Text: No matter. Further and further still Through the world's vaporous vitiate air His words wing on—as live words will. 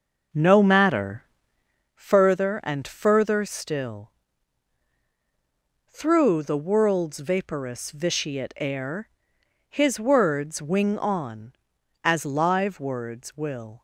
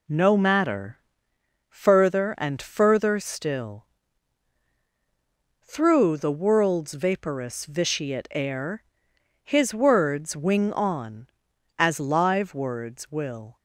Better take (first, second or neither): second